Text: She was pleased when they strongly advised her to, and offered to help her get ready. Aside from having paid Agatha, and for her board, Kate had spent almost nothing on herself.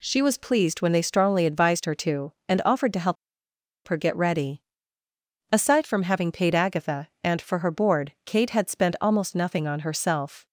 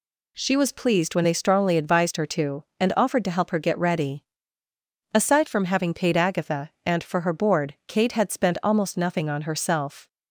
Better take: second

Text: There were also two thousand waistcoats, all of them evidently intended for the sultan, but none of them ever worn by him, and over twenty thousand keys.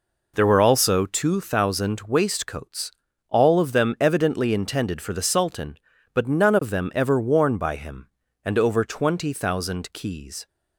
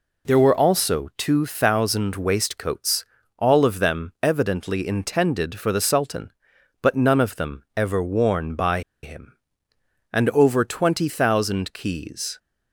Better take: first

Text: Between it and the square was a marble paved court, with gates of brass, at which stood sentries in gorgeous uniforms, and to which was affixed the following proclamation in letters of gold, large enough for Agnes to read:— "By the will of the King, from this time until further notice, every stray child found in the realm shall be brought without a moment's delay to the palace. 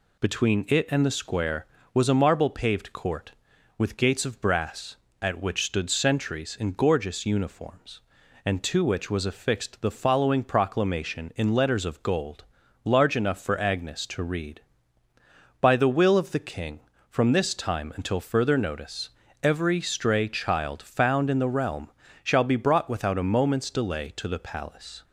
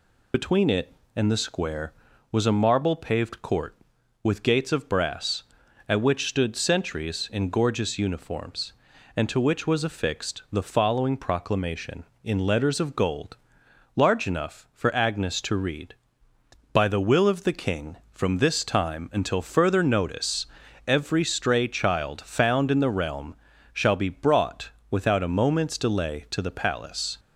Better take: first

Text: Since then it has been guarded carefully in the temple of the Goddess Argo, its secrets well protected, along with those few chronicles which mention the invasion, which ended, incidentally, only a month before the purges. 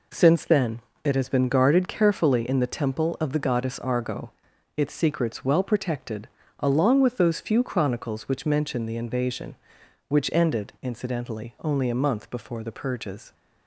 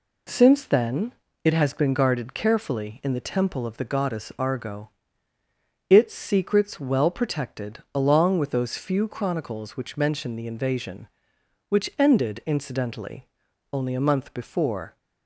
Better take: first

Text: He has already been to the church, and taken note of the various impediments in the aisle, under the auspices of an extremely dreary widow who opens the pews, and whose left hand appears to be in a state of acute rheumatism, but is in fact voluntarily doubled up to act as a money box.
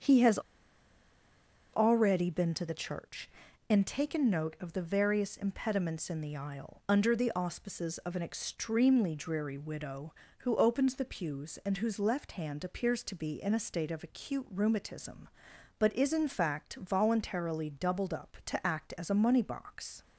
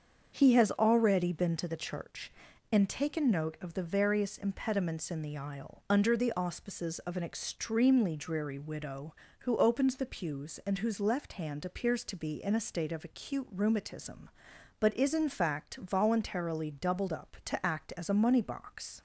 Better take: second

